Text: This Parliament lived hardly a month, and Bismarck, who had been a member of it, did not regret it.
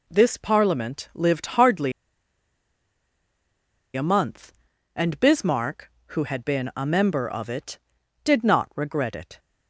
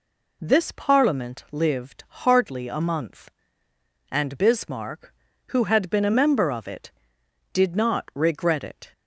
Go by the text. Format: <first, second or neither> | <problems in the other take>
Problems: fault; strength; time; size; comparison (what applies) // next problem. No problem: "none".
second | pauses between "hardly" and "a"; strong; at 1.9 s; 2.0 s long